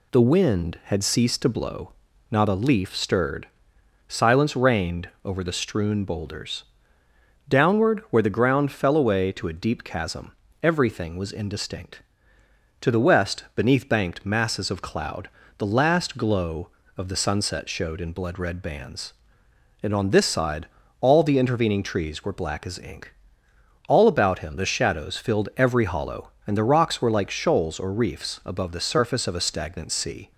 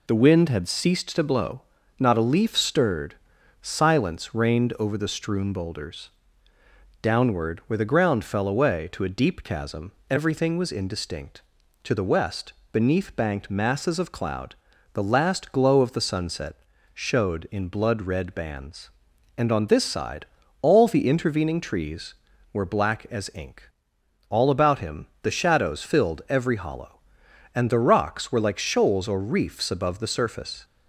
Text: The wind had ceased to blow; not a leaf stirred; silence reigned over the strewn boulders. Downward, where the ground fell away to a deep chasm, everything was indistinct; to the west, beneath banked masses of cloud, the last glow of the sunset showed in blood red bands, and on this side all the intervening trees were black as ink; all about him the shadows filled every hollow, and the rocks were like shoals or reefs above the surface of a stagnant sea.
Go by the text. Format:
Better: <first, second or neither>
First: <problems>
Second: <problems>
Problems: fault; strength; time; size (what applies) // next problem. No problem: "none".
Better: first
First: pauses between "side" and "all"; slight; at 20.6 s; 0.36 s long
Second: pauses between "sunset" and "showed"; at 16.5 s; 0.38 s long // pauses between "side" and "all"; slight; at 20.2 s; 0.36 s long // pauses between "him" and "the"; slight; at 25.0 s; 0.16 s long // stops before "of a stagnant sea"; at 30.6 s